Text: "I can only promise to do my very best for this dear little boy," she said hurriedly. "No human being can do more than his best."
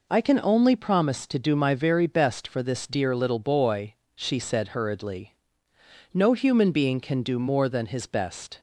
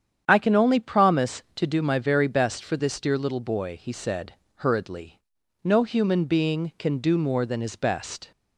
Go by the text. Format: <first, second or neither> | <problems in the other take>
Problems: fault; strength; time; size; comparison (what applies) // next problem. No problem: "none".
first | starts louder than the rest; strong; until 1.2 s; 8.5 dB // says "he" for "she"; at 3.7 s // pauses between "said" and "hurriedly"; slight; at 4.3 s; 0.22 s long